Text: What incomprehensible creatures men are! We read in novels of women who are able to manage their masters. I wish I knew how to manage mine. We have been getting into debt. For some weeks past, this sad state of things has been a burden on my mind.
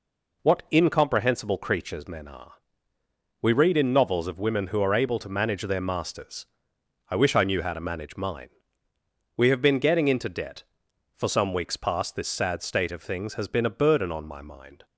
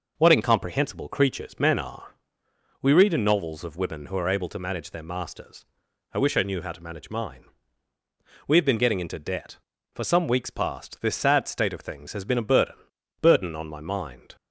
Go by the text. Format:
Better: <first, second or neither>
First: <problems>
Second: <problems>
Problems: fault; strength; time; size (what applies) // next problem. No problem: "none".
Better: first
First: none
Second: says "burden" twice; at 13.2 s